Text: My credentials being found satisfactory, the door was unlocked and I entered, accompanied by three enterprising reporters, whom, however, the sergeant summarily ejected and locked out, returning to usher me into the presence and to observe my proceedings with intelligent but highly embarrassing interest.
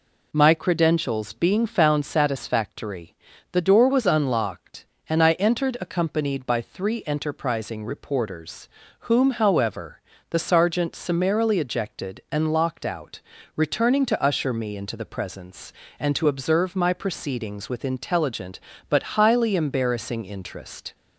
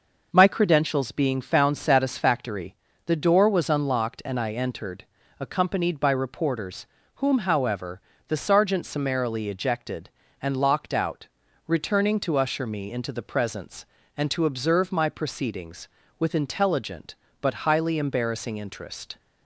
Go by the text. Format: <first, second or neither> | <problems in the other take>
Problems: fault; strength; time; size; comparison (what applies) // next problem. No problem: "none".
first | skips "three enterprising"; at 6.1 s